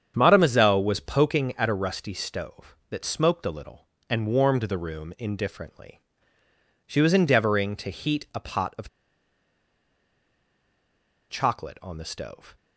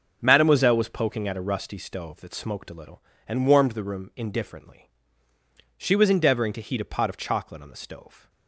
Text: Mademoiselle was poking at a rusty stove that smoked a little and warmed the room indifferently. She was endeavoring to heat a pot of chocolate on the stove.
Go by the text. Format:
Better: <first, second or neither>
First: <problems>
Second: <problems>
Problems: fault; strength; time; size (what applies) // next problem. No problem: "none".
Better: second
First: starts louder than the rest; strong; until 1.1 s; 8 dB // pauses between "of" and "chocolate"; strong; at 8.8 s; 2.4 s long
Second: starts louder than the rest; noticeable; until 1.2 s; 6 dB